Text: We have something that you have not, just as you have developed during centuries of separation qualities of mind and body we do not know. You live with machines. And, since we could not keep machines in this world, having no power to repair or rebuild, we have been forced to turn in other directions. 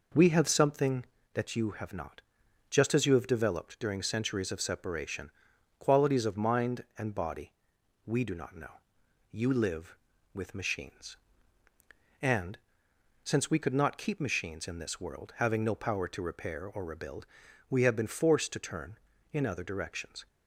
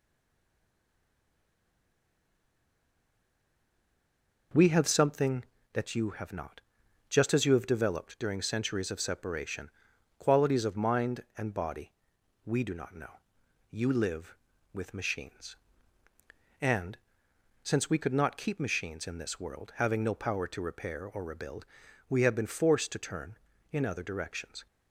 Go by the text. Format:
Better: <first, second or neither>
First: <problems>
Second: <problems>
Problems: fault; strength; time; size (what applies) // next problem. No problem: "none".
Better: first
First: pauses between "separation" and "qualities"; noticeable; at 5.3 s; 0.48 s long // pauses between "body" and "we"; noticeable; at 7.5 s; 0.52 s long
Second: stays silent before the first word; strong; until 4.5 s; 4.5 s long // pauses between "separation" and "qualities"; noticeable; at 9.7 s; 0.48 s long // pauses between "body" and "we"; noticeable; at 11.9 s; 0.52 s long